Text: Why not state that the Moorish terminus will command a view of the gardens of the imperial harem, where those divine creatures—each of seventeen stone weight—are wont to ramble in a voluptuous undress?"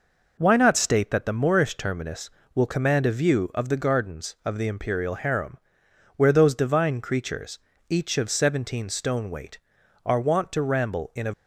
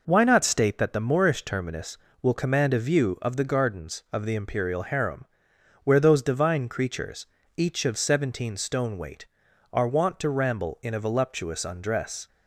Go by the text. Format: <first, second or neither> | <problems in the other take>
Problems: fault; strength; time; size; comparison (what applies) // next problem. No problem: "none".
second | stops before "voluptuous undress"; at 11.3 s